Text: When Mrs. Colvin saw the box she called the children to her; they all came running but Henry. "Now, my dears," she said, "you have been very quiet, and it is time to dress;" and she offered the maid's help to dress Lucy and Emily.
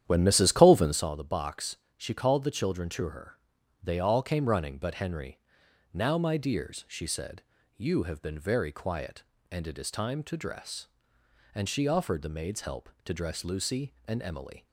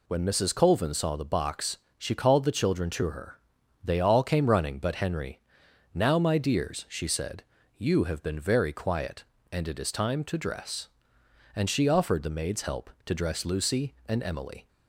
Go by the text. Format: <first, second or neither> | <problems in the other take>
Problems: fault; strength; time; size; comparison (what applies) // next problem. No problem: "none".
second | starts louder than the rest; strong; until 1.1 s; 10.5 dB // pauses between "box" and "she"; slight; at 1.7 s; 0.20 s long; slight in the second